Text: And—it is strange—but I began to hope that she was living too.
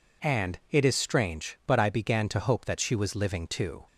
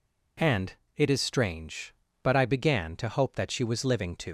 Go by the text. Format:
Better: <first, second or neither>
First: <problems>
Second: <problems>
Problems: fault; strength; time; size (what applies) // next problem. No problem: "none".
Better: first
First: none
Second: leaves "too" unfinished; at 4.2 s; 110 ms